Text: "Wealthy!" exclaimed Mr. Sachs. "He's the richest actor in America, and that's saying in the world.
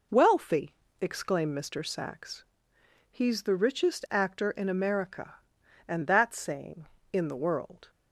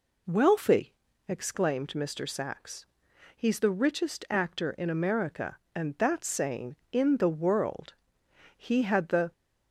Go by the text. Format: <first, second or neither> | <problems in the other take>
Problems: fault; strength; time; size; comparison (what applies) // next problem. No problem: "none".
first | goes on to say "He had the"; noticeable; from 8.5 s on; 0.76 s long